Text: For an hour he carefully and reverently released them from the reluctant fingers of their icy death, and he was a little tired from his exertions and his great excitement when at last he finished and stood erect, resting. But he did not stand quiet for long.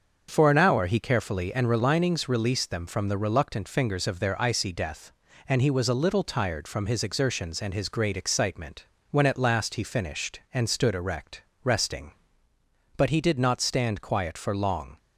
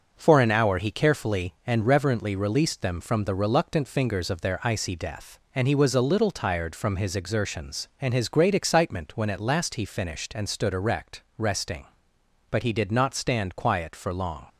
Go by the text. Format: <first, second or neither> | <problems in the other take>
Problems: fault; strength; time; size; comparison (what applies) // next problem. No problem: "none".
second | starts louder than the rest; until 1.3 s; 6.5 dB; also in the second // says "relinings" for "reverently"; at 1.6 s // pauses between "excitement" and "when"; slight; at 8.8 s; 0.24 s long